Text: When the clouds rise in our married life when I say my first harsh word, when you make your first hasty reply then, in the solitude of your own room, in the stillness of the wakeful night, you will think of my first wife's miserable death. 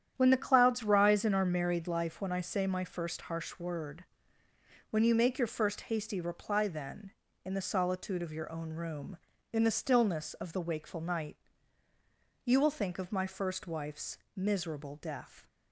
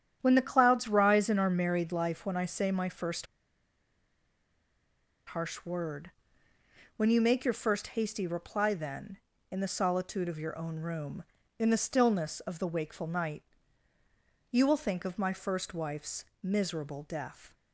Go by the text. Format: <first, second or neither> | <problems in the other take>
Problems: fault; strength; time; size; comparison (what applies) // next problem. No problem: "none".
first | starts louder than the rest; strong; until 1.2 s; 9.5 dB; strong in the first // pauses between "first" and "harsh"; strong; at 3.2 s; 2.0 s long // pauses between "wife's" and "miserable"; slight; at 16.2 s; 0.18 s long; slight in the first